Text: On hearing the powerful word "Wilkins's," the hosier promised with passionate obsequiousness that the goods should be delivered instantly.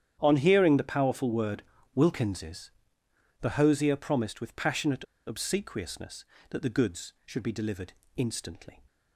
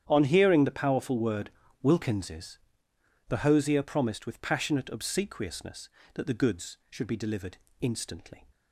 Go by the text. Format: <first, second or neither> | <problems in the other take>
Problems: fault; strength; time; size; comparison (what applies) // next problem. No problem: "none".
second | starts louder than the rest; strong; until 1.2 s; 9.5 dB; strong in the second // pauses between "word" and "Wilkins's"; slight; at 1.6 s; 0.32 s long; slight in the second // pauses between "passionate" and "obsequiousness"; slight; at 5.0 s; 0.21 s long // pauses between "delivered" and "instantly"; slight; at 7.9 s; 0.24 s long; slight in the second